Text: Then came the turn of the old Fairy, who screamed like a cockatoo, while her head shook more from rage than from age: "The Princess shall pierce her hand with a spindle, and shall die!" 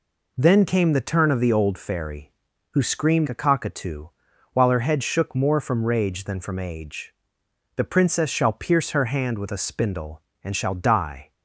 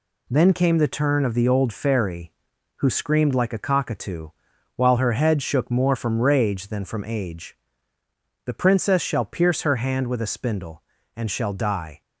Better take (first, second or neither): second